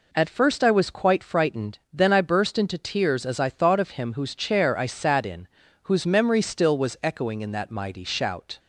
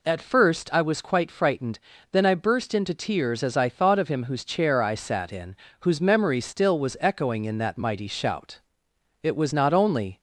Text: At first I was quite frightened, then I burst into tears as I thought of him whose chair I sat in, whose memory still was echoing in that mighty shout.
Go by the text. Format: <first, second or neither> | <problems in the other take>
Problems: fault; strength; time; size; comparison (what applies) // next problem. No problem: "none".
first | goes on to say "It was not only"; noticeable; from 9.2 s on; 1.0 s long